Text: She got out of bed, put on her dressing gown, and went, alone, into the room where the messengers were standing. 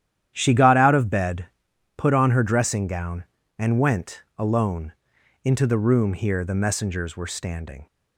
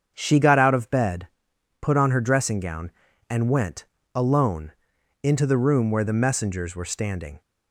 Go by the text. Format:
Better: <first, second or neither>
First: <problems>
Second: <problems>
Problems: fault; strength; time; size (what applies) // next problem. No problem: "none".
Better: second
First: starts louder than the rest; strong; until 1.3 s; 10.5 dB // says "here" for "where"; at 6.1 s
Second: starts louder than the rest; strong; until 1.1 s; 7.5 dB